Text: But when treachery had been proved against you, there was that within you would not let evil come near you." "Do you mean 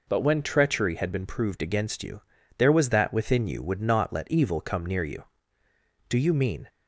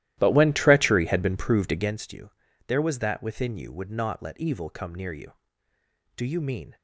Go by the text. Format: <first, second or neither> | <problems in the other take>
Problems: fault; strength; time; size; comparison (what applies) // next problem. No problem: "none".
first | starts louder than the rest; strong; until 2.0 s; 14.5 dB